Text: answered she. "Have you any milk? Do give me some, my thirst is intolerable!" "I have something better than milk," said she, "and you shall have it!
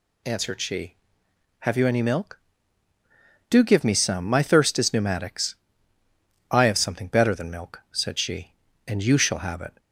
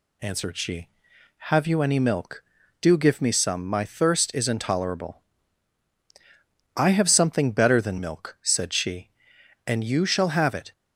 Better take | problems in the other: second | says "pneumatics" for "intolerable"; at 4.9 s

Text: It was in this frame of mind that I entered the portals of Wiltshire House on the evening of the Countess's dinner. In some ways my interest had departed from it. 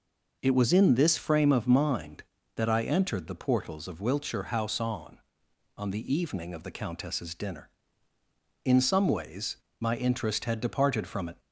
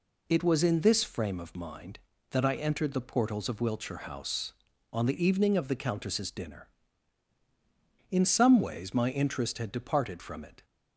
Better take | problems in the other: second | says "on" twice; at 5.7 s // pauses between "ways" and "my"; slight; at 9.5 s; 0.24 s long

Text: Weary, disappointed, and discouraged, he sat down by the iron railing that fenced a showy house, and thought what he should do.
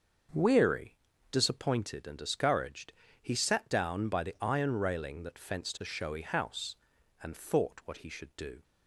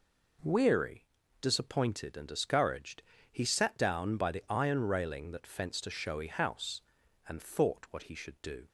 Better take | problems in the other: second | starts louder than the rest; until 1.6 s; 6.5 dB

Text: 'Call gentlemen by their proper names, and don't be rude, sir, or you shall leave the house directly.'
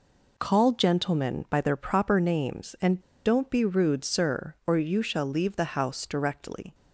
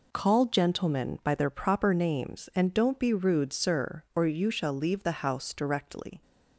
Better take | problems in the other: second | pauses between "and" and "don't"; slight; at 3.0 s; 0.24 s long

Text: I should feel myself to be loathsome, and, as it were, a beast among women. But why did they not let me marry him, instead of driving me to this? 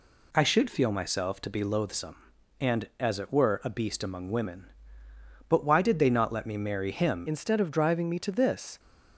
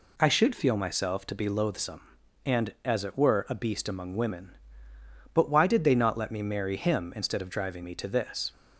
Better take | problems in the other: second | changes voice at "instead"; from 7.2 s on; 1.5 s long

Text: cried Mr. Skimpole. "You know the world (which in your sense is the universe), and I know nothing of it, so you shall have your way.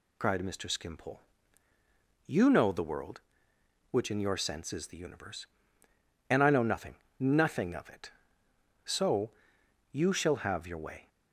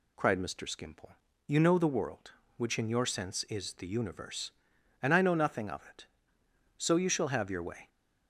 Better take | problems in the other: second | says "nothing" twice; at 7.1 s // pauses between "so" and "you"; noticeable; at 9.3 s; 0.58 s long

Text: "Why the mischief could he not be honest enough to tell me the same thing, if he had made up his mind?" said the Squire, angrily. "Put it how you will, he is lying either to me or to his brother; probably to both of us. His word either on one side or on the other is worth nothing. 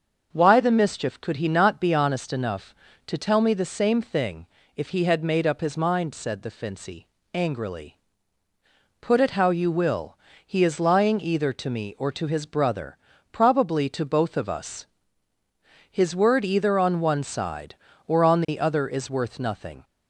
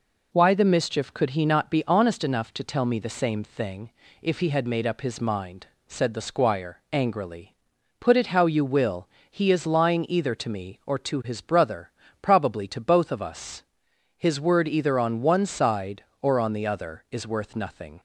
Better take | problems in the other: second | starts louder than the rest; until 1.3 s; 6.5 dB // says "Fincy" for "Squire"; at 6.5 s

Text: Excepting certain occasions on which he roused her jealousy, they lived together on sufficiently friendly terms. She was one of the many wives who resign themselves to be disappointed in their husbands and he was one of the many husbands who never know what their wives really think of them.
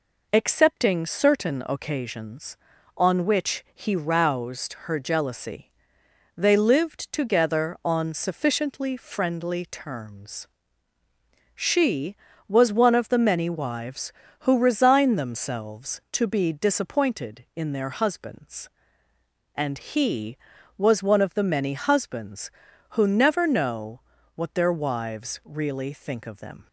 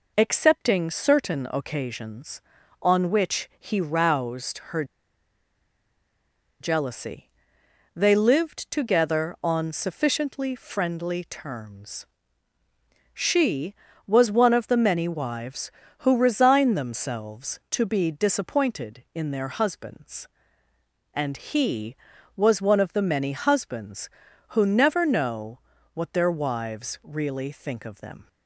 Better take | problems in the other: first | pauses between "her" and "jealousy"; strong; at 4.8 s; 1.7 s long // pauses between "know" and "what"; slight; at 25.5 s; 0.36 s long; slight in the first

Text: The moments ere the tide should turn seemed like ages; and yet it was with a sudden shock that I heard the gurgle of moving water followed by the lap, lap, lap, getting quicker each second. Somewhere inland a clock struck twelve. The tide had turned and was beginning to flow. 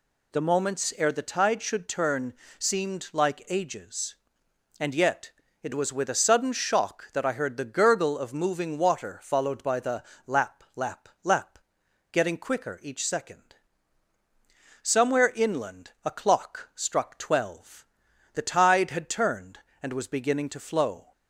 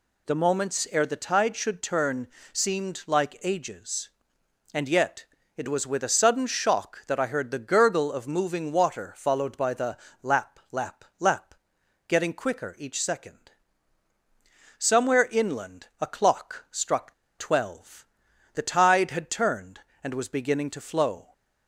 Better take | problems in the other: first | pauses between "turn" and "seemed"; slight; at 2.2 s; 0.22 s long; slight in the first // pauses between "yet" and "it"; slight; at 5.2 s; 0.32 s long; slight in the first // pauses between "the" and "lap"; slight; at 9.9 s; 0.24 s long; slight in the first // pauses between "struck" and "twelve"; slight; at 17.1 s; 0.26 s long

